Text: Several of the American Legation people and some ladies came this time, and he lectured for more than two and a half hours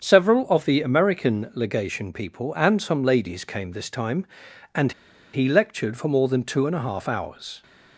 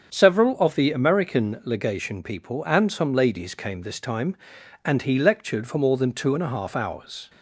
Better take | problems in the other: second | starts louder than the rest; until 1.0 s; 7 dB; strong in the second // pauses between "and" and "he"; at 4.9 s; 0.41 s long

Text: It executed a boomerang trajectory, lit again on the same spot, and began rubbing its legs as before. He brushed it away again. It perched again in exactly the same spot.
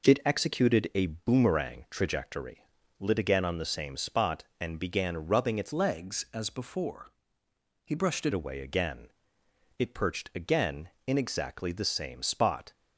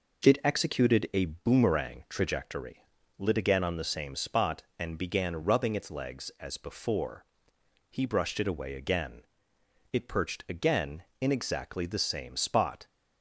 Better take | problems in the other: second | changes voice from "legs" to "it"; from 5.7 to 8.3 s; 2.6 s long

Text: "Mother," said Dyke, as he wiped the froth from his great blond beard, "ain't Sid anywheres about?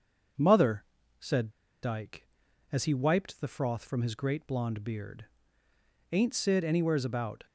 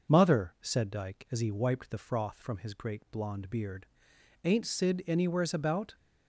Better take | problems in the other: second | starts louder than the rest; until 2.0 s; 6.5 dB // pauses between "said" and "Dyke"; slight; at 1.5 s; 0.31 s long

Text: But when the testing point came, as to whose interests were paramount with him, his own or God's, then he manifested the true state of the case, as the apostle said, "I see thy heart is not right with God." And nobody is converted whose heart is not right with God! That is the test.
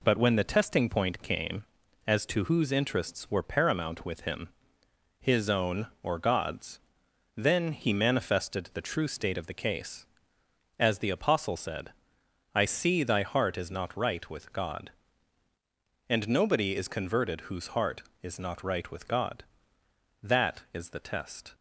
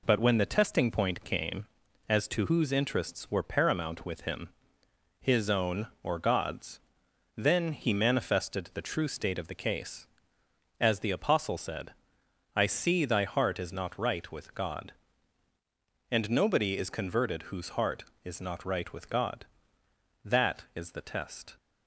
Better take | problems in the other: neither | none

